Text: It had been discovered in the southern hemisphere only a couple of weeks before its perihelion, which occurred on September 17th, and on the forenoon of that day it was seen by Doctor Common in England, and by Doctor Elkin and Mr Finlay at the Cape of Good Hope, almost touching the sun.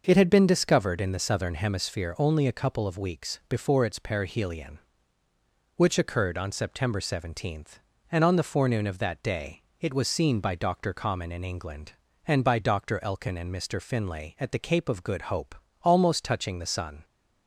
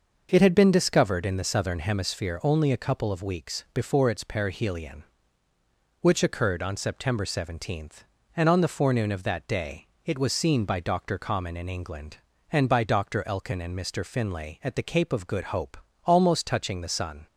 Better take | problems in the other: neither | pauses between "day" and "it"; slight; the same in both

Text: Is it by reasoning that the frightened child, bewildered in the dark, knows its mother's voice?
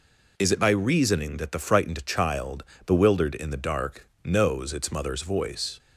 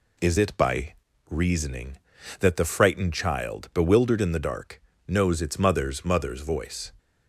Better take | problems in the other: first | pauses between "by" and "reasoning"; slight; at 0.9 s; 0.36 s long // says "mother's" twice; at 6.0 s

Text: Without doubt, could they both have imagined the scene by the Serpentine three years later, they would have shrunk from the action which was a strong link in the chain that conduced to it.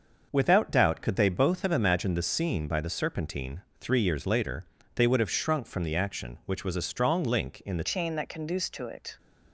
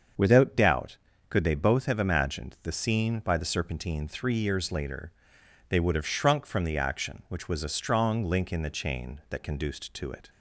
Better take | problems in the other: second | starts louder than the rest; until 1.3 s; 6 dB; also in the second // pauses between "Serpentine" and "three"; slight; at 3.6 s; 0.20 s long // changes voice at "chain"; from 7.8 s on; 1.3 s long

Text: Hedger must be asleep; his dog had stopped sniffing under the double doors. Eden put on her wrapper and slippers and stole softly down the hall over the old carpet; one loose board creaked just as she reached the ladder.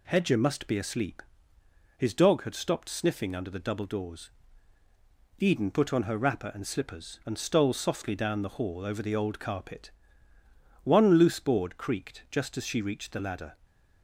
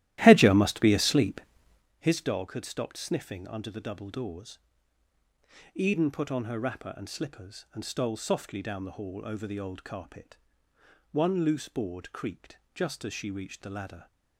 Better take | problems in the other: first | starts louder than the rest; strong; until 1.9 s; 14 dB // pauses between "creaked" and "just"; slight; at 12.5 s; 0.18 s long

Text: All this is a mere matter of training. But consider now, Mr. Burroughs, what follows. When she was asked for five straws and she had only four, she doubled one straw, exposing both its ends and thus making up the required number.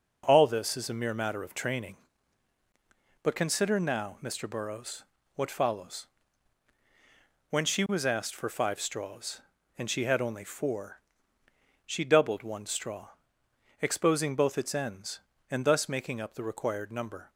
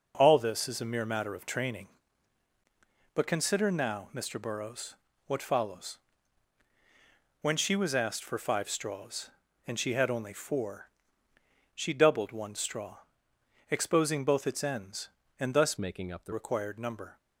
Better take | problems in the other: first | changes voice from "making" to "the"; from 15.7 to 16.3 s; 0.6 s long

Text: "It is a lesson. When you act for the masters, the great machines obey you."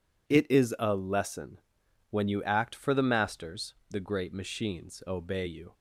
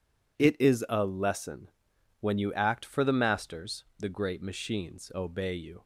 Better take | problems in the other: neither | none

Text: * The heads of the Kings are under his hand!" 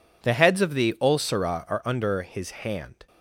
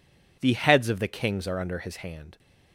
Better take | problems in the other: second | says "Ulcera" for "Kings"; at 1.0 s

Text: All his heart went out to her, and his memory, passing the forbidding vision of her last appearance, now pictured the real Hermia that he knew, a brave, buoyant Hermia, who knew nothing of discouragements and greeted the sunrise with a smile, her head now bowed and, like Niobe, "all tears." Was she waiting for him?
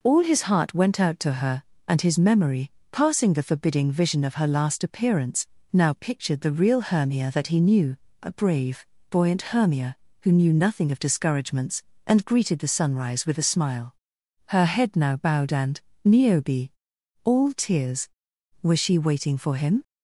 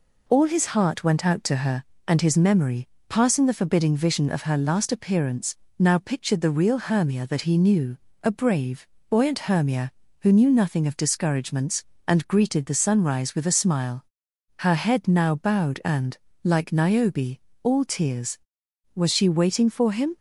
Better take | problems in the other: second | skips "like"; at 15.9 s

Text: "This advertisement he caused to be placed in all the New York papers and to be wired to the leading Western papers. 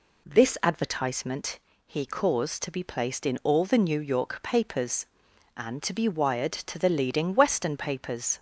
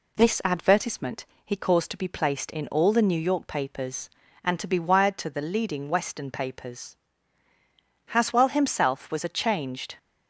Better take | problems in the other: first | pauses between "advertisement" and "he"; slight; at 1.2 s; 0.18 s long; slight in the first // goes on to say "Haswell himself was a changed"; strong; from 8.0 s on; 1.9 s long

